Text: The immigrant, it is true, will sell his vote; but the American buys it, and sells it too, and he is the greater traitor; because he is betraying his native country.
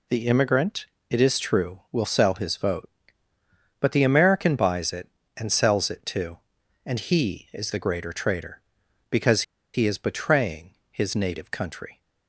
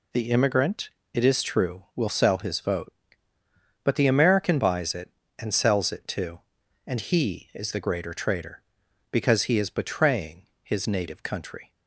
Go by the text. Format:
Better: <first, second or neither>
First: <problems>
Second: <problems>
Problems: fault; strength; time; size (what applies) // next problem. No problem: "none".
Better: second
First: pauses between "because" and "he"; slight; at 9.4 s; 0.32 s long // pauses between "betraying" and "his"; slight; at 10.7 s; 0.16 s long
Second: pauses between "betraying" and "his"; slight; at 10.4 s; 0.16 s long